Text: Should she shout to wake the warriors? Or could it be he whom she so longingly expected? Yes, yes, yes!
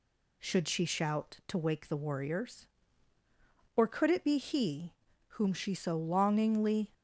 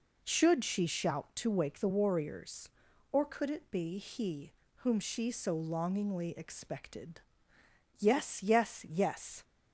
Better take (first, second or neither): second